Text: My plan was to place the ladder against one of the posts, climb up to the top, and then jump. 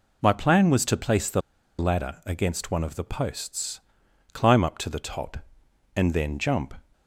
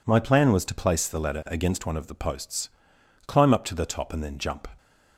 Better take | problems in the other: second | pauses between "the" and "ladder"; at 1.4 s; 0.38 s long

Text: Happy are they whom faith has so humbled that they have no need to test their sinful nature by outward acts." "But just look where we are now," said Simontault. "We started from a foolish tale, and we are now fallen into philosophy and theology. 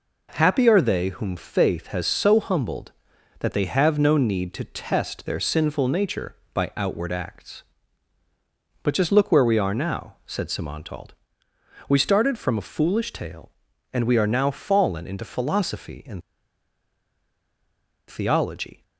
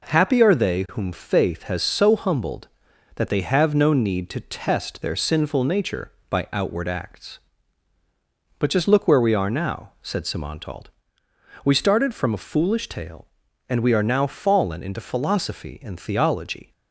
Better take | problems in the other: second | pauses between "and" and "theology"; strong; at 16.2 s; 1.8 s long

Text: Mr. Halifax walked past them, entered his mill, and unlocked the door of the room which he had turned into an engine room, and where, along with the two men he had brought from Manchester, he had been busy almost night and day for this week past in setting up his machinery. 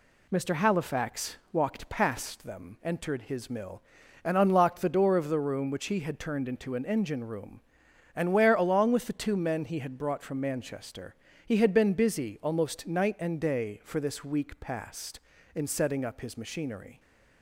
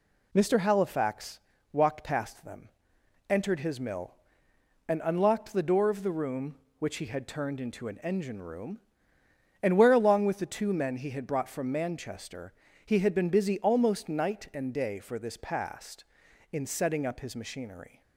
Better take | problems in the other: first | pauses between "Halifax" and "walked"; slight; at 1.3 s; 0.34 s long; slight in the first // skips "week"; at 15.3 s

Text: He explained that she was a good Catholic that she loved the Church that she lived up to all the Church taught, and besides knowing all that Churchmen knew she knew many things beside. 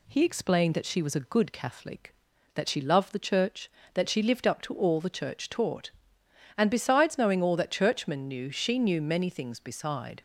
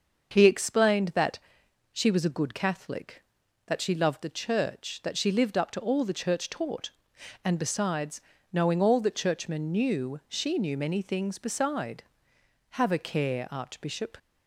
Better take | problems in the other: first | starts louder than the rest; until 1.3 s; 6.5 dB // pauses between "that" and "she"; noticeable; at 1.3 s; 0.54 s long // pauses between "besides" and "knowing"; slight; at 8.2 s; 0.28 s long // goes on to say "Have a care Archbishop"; from 12.6 s on; 1.4 s long

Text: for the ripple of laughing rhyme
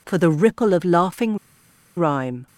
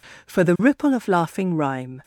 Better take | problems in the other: second | pauses between "laughing" and "rhyme"; noticeable; at 1.3 s; 0.60 s long

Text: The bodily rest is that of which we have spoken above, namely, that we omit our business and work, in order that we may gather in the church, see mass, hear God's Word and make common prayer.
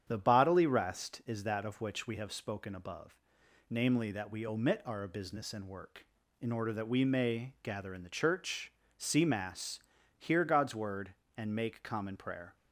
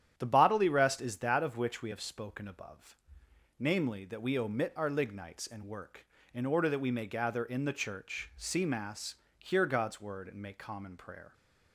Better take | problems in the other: first | starts louder than the rest; strong; until 1.1 s; 10 dB; strong in the first // says "lignites" for "business"; at 4.8 s

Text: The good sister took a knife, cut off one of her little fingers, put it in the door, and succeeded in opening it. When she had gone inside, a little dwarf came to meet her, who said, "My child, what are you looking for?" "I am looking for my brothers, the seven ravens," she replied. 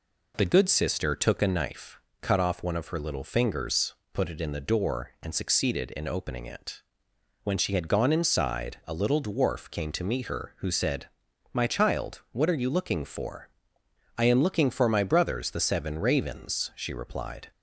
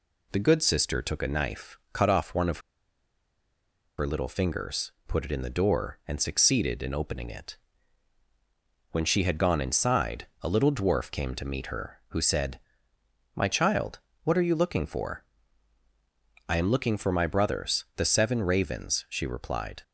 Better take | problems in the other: first | pauses between "of" and "her"; strong; at 2.5 s; 1.3 s long

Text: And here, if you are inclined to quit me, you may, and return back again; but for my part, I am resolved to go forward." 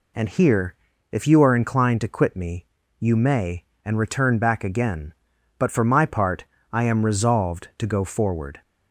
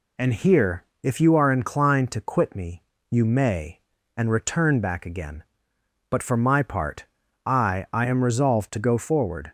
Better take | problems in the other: first | says "I" twice; at 7.9 s

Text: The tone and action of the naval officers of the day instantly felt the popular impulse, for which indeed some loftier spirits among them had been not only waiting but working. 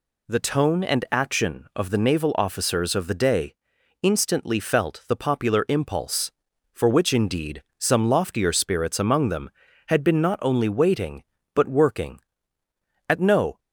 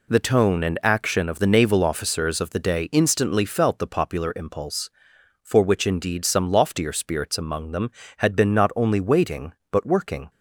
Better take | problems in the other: second | pauses between "day" and "instantly"; noticeable; at 3.5 s; 0.48 s long // pauses between "indeed" and "some"; slight; at 7.6 s; 0.16 s long // goes on to say "At no"; from 13.0 s on; 0.52 s long

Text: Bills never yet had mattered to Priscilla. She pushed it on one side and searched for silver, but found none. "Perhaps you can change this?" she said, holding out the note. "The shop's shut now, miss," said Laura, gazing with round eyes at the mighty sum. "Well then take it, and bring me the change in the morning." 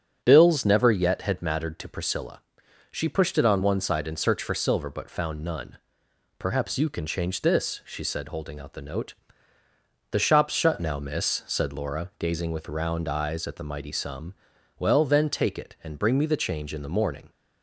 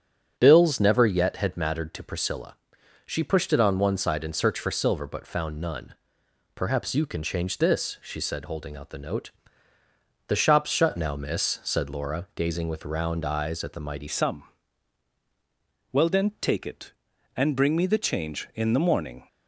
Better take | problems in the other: first | starts louder than the rest; strong; until 1.3 s; 8 dB; strong in the first // changes voice at "sum"; from 14.0 s on; 5.2 s long

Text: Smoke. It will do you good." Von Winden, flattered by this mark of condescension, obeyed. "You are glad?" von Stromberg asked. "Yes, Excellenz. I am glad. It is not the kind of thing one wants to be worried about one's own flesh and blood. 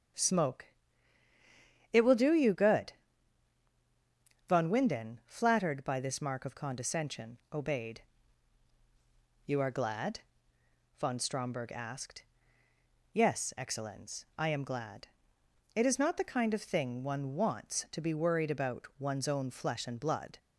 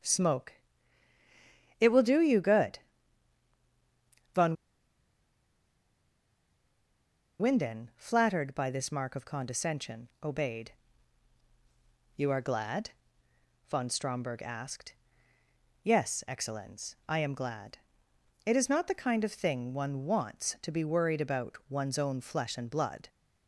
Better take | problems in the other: first | starts louder than the rest; strong; until 2.2 s; 7 dB; also in the first // pauses between "Von" and "Winden"; strong; at 4.5 s; 2.8 s long

